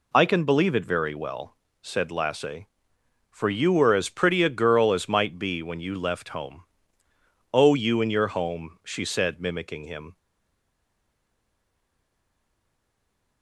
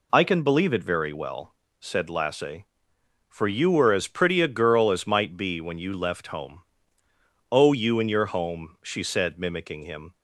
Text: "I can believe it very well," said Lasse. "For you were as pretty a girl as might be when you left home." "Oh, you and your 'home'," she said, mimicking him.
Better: second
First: stays silent after the last word; strong; from 10.1 s on; 3.3 s long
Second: none

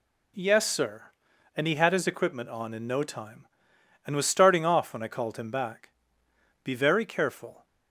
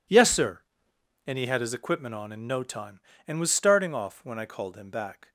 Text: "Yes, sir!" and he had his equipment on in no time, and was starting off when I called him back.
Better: second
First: goes on to say "Be very careful"; noticeable; from 6.6 s on; 1.0 s long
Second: none

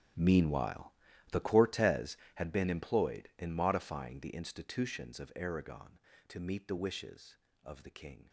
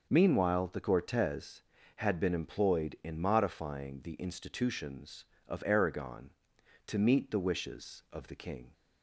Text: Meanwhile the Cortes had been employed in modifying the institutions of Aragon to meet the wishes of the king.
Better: second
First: gets quieter; strong; throughout; 18 dB // pauses between "Meanwhile" and "the"; at 0.9 s; 0.38 s long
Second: none

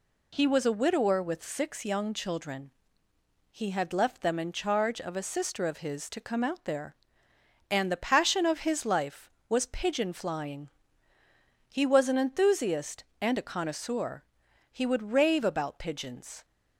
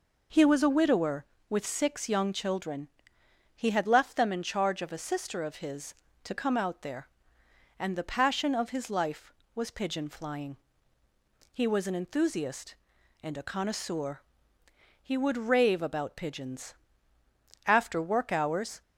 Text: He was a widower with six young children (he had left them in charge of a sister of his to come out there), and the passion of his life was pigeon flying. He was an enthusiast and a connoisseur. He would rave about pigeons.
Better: first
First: none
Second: goes on to say "After work hours"; noticeable; from 17.6 s on; 1.1 s long

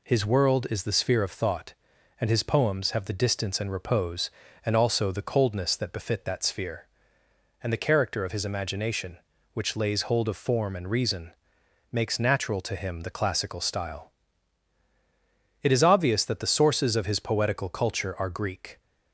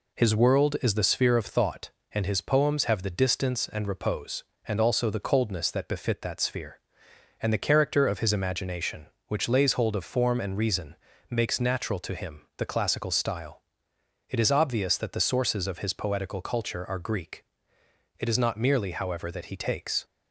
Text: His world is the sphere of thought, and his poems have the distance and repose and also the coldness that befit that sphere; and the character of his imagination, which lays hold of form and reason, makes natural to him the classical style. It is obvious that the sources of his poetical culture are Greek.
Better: first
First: none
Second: pauses between "him" and "the"; slight; at 12.4 s; 0.16 s long // goes on to say "It is not merely however that he takes"; strong; from 18.1 s on; 1.8 s long

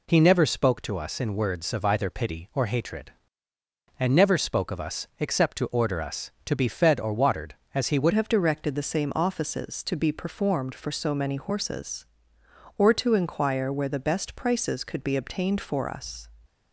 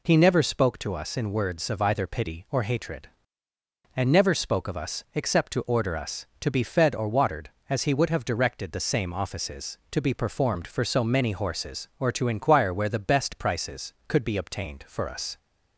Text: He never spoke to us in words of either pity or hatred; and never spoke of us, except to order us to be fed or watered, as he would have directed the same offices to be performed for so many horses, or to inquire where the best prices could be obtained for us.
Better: second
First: changes voice at "have"; from 8.1 s on; 8.1 s long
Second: none

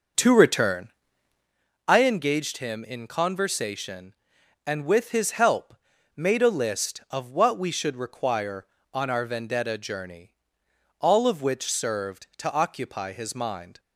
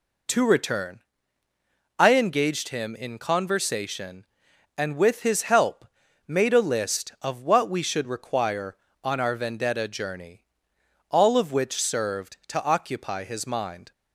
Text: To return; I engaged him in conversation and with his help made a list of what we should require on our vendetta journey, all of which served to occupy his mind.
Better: second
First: starts louder than the rest; noticeable; until 1.5 s; 6 dB // pauses between "help" and "made"; at 5.7 s; 0.40 s long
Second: pauses between "help" and "made"; at 5.8 s; 0.40 s long

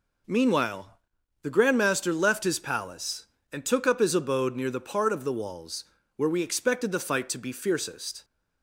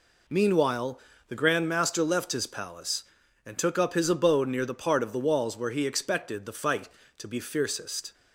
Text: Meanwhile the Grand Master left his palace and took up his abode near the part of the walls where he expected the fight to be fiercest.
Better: second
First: pauses between "Meanwhile" and "the"; noticeable; at 0.8 s; 0.54 s long // pauses between "walls" and "where"; slight; at 5.8 s; 0.34 s long // says "we" for "he"; at 6.2 s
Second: pauses between "Meanwhile" and "the"; slight; at 0.9 s; 0.28 s long

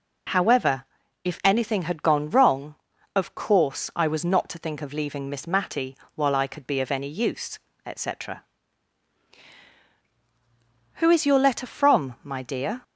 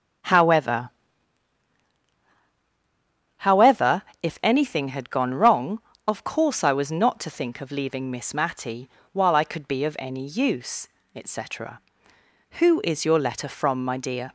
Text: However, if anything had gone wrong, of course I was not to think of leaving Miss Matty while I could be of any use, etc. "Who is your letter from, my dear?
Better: first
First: pauses between "Matty" and "while"; slight; at 5.9 s; 0.20 s long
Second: starts louder than the rest; strong; until 3.6 s; 9 dB // says "However" twice; at 3.3 s // pauses between "Matty" and "while"; slight; at 8.8 s; 0.24 s long

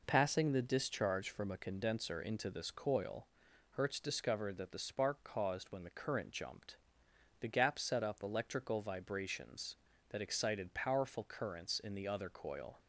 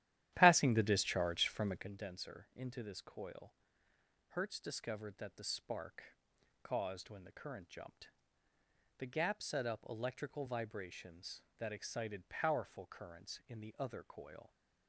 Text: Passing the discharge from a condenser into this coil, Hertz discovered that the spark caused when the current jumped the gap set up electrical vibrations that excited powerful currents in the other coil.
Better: first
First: pauses between "jumped" and "the"; noticeable; at 6.7 s; 0.64 s long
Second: starts louder than the rest; strong; until 1.9 s; 12.5 dB // pauses between "spark" and "caused"; noticeable; at 6.1 s; 0.46 s long // pauses between "jumped" and "the"; noticeable; at 8.0 s; 0.90 s long

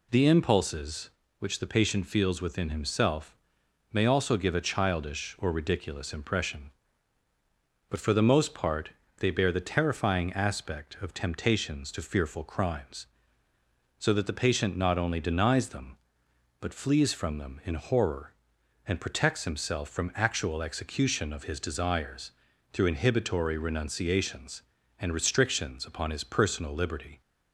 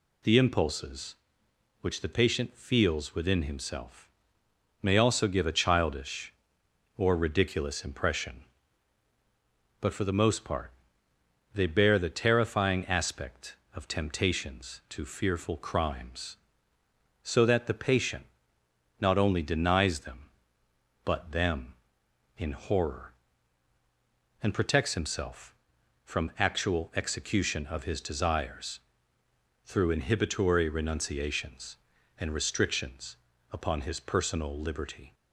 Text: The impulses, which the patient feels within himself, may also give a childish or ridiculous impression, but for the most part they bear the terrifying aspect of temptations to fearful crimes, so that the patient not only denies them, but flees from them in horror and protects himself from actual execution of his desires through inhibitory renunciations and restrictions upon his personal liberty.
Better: first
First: pauses between "part" and "they"; slight; at 8.8 s; 0.30 s long // pauses between "desires" and "through"; at 22.3 s; 0.42 s long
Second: pauses between "part" and "they"; noticeable; at 10.7 s; 0.82 s long // pauses between "patient" and "not"; noticeable; at 18.2 s; 0.78 s long // skips "flees from"; at 21.3 s // pauses between "desires" and "through"; noticeable; at 28.7 s; 0.86 s long // pauses between "restrictions" and "upon"; slight; at 33.1 s; 0.34 s long

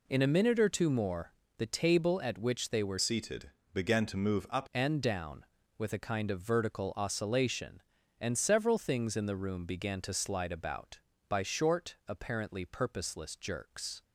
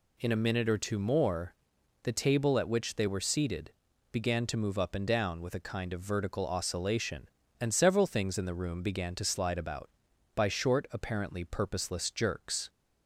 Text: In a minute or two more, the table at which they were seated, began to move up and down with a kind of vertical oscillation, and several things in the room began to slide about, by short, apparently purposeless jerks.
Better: second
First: changes voice from "seated" to "up"; from 3.0 to 4.6 s; 1.6 s long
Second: none

